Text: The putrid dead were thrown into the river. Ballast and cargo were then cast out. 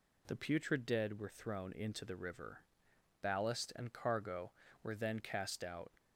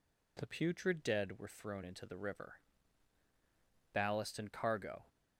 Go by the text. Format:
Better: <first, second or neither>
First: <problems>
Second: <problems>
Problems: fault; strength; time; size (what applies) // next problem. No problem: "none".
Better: first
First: none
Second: stops before "were then cast out"; at 5.0 s